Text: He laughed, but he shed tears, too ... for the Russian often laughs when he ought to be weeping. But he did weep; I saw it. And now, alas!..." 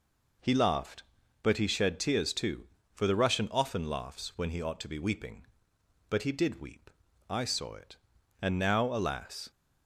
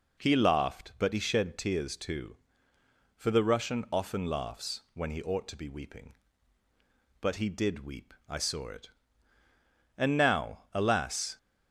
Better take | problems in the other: neither | none

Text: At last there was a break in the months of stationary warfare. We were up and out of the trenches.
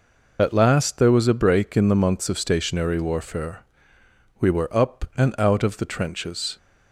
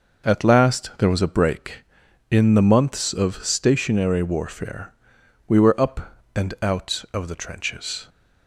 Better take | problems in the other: second | loses the start of "At"; at 0.3 s; 75 ms

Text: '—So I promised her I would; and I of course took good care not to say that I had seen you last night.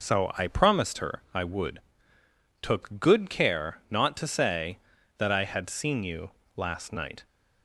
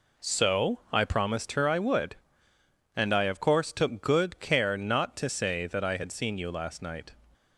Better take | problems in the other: second | skips "and I of course"; at 2.1 s // pauses between "you" and "last"; slight; at 6.3 s; 0.25 s long

